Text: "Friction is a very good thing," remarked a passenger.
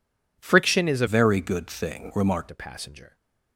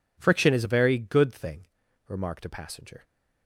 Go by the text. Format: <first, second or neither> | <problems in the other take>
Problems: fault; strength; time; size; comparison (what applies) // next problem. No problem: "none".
second | changes voice from "very" to "remarked"; from 1.0 to 2.5 s; 1.5 s long